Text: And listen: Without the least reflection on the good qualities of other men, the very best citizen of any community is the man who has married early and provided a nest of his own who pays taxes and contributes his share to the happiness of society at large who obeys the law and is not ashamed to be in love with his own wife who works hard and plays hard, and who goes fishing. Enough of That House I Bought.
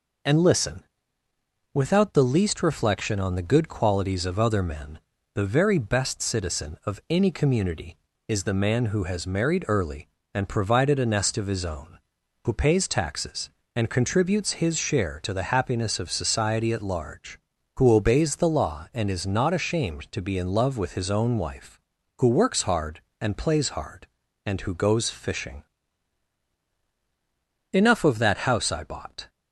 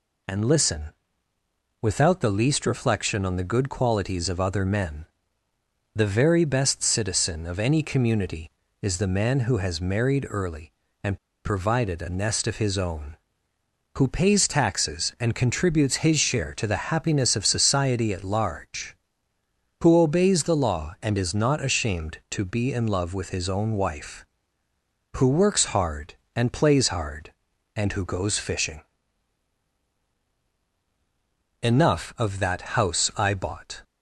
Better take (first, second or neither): first